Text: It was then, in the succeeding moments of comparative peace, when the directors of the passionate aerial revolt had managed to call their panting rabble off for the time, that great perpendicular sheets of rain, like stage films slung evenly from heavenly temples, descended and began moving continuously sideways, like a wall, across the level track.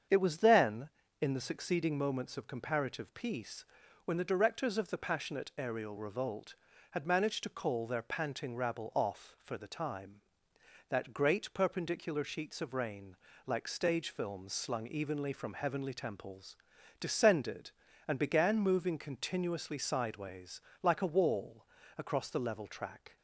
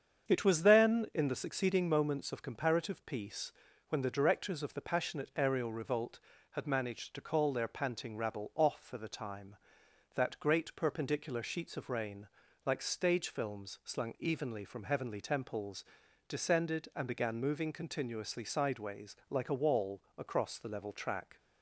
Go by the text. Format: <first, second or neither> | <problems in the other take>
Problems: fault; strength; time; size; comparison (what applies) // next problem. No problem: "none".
neither | starts louder than the rest; strong; the same in both